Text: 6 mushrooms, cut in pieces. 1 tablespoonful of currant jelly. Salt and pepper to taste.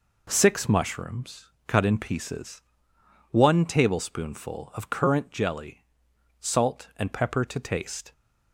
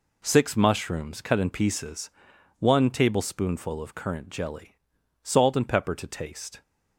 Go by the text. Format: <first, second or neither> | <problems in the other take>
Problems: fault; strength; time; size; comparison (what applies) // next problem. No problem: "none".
neither | none